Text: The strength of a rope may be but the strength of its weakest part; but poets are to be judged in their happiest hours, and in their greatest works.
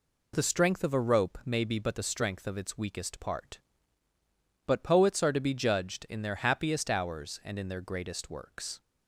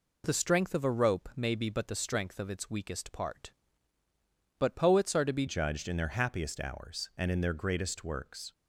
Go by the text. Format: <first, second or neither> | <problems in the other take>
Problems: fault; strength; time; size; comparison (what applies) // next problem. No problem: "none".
first | changes voice at "judged"; from 5.4 s on; 3.1 s long